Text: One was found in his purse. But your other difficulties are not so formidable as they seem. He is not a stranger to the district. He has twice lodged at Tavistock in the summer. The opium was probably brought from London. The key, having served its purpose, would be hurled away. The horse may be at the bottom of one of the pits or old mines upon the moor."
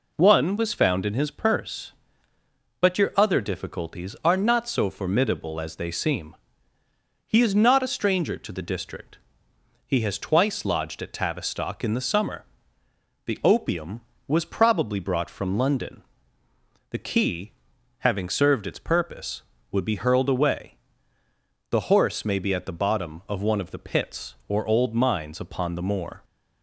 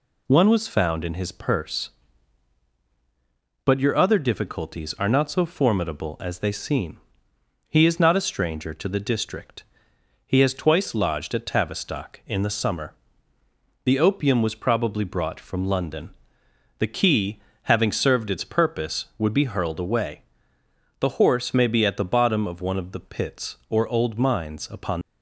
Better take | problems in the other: first | stops before "the moor"; at 25.0 s

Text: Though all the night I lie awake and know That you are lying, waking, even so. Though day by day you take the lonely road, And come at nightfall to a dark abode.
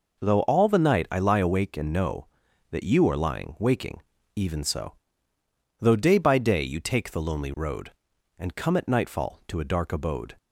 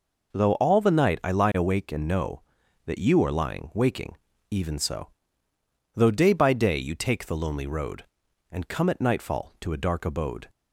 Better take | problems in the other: neither | none

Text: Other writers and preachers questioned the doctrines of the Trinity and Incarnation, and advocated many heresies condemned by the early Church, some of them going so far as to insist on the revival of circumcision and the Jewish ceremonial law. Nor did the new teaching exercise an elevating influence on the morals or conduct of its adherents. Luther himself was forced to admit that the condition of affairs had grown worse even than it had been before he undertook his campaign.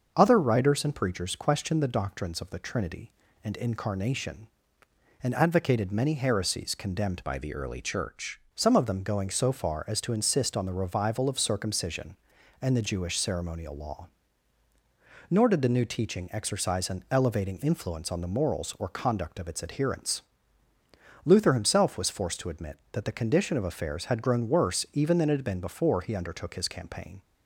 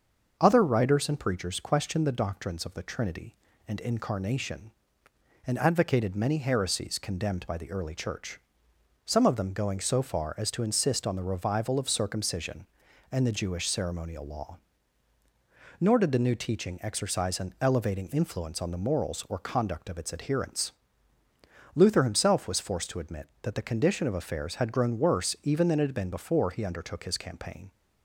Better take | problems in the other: second | starts louder than the rest; until 1.1 s; 6.5 dB; also in the second // changes voice from "by" to "Church"; from 7.2 to 8.4 s; 1.2 s long

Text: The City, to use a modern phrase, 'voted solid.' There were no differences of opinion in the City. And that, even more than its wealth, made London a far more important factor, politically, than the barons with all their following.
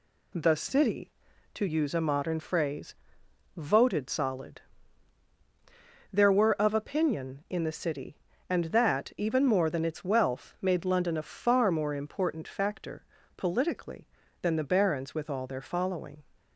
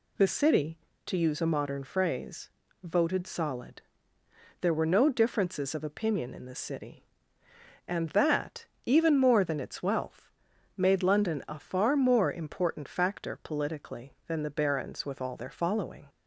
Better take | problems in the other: second | skips "no differences"; at 6.5 s

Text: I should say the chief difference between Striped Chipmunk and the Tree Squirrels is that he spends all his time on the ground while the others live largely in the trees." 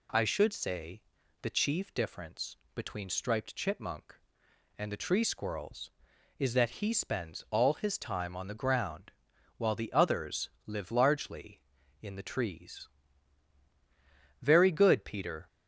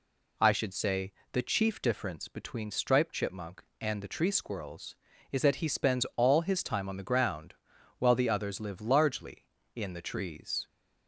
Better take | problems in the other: second | pauses between "say" and "the"; at 1.0 s; 0.40 s long; slight in the second // pauses between "difference" and "between"; slight; at 2.5 s; 0.18 s long // pauses between "ground" and "while"; at 9.1 s; 0.44 s long; noticeable in the second // pauses between "others" and "live"; slight; at 10.4 s; 0.18 s long // goes on to say "Very good Peter"; noticeable; from 14.4 s on; 1.0 s long

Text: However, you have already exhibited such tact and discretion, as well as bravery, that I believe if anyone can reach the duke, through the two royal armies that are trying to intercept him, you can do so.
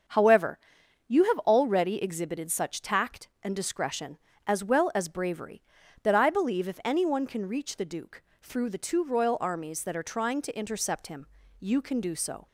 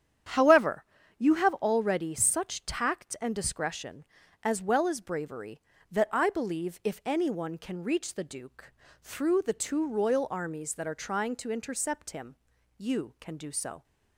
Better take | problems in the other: first | starts louder than the rest; strong; until 1.6 s; 9 dB; also in the first // skips "exhibited"; at 2.1 s

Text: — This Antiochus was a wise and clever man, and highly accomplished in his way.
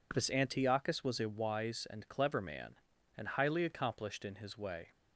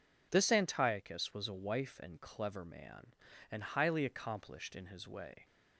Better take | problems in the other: first | says "wife" for "wise"; at 1.5 s

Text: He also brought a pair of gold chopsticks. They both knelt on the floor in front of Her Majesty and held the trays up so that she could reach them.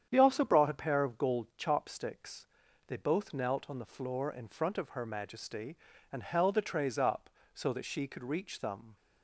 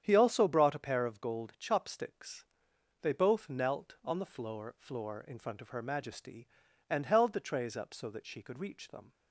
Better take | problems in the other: first | starts louder than the rest; strong; until 1.0 s; 9 dB; strong in the first // says "floor" twice; at 4.7 s

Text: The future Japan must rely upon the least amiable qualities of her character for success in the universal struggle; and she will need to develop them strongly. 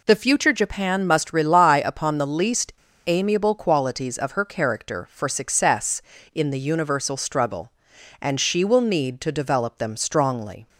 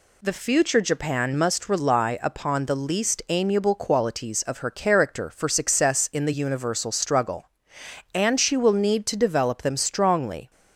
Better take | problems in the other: second | pauses between "least" and "amiable"; slight; at 2.7 s; 0.33 s long

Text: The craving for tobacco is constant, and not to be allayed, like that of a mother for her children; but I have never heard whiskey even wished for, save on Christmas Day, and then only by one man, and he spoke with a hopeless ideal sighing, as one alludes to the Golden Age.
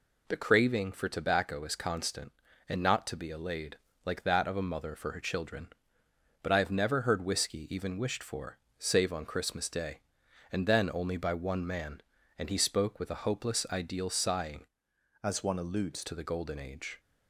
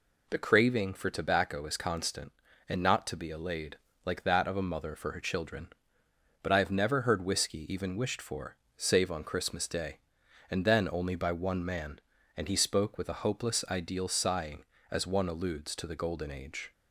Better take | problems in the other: second | changes voice from "as" to "alludes"; from 15.2 to 16.0 s; 0.8 s long

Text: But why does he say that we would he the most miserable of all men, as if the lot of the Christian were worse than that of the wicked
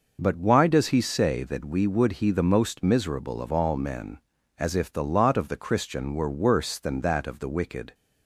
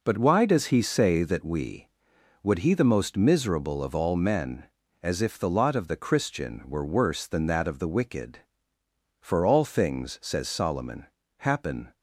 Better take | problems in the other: first | goes on to say "For all things says Solomon happen"; strong; from 9.1 s on; 2.7 s long

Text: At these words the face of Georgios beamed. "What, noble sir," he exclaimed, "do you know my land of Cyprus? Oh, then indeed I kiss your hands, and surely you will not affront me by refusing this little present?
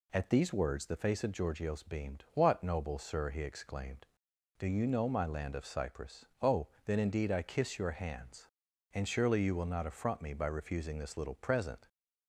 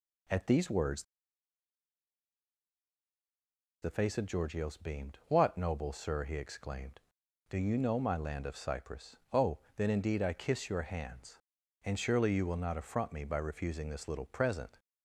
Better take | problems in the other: first | pauses between "words" and "the"; strong; at 1.0 s; 2.7 s long

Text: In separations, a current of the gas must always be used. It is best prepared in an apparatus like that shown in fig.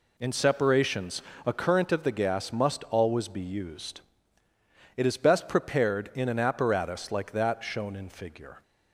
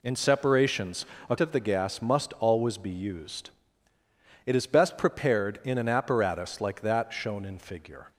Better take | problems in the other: first | skips "current"; at 1.3 s

